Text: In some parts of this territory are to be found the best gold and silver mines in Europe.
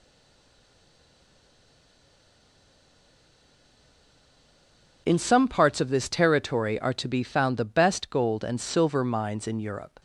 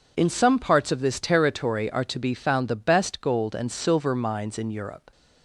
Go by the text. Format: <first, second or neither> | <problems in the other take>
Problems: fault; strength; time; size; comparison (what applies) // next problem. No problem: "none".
second | stays silent before the first word; strong; until 5.0 s; 5.0 s long